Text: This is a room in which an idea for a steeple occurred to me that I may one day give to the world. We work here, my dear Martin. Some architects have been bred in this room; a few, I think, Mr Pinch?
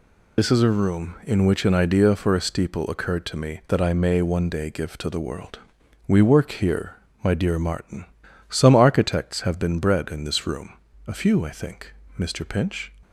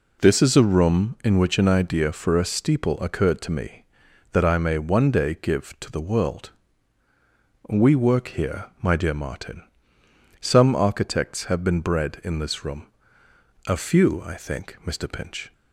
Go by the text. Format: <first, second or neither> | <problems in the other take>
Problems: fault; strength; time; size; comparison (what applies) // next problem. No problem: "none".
second | loses the start of "This"; at 0.3 s; 60 ms